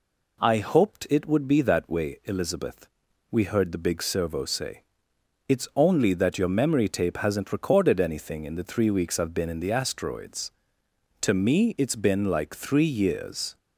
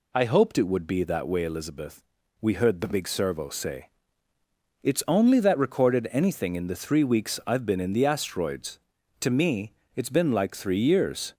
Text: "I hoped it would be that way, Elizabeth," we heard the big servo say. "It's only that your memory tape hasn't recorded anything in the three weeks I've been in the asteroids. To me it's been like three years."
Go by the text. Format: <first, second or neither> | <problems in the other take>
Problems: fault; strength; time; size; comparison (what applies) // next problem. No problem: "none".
first | skips "your memory tape hasn't"; at 5.5 s // pauses between "me" and "it's"; slight; at 9.7 s; 0.22 s long